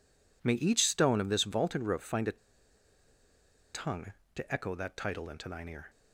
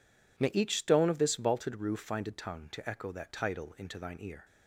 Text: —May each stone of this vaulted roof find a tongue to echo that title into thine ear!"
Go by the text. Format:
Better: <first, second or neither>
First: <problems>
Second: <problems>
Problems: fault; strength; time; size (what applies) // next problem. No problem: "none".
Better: second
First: pauses between "a" and "tongue"; strong; at 2.3 s; 1.3 s long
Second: none